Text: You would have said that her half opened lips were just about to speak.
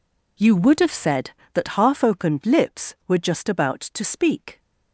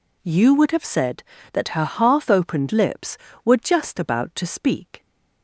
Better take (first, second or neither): second